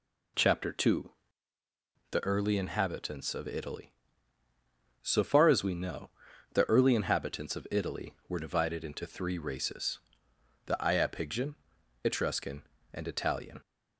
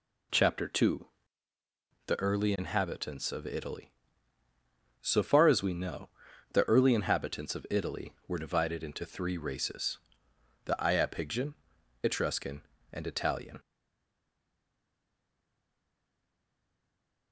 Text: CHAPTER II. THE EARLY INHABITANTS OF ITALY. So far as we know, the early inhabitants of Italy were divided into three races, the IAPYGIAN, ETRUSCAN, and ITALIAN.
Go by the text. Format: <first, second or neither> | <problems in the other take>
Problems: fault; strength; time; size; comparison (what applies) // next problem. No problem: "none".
first | stays silent after the last word; strong; from 13.5 s on; 3.8 s long